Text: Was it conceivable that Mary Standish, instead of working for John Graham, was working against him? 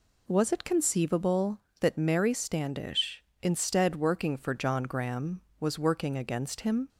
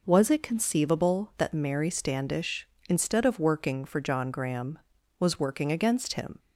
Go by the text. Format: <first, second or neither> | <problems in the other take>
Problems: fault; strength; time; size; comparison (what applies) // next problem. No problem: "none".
second | skips "of"; at 3.9 s